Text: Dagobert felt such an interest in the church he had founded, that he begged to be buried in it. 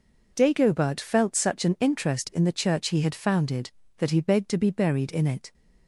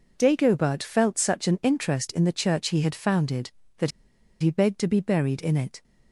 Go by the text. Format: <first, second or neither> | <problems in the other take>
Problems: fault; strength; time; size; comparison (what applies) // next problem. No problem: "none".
first | pauses between "that" and "he"; noticeable; at 3.9 s; 0.50 s long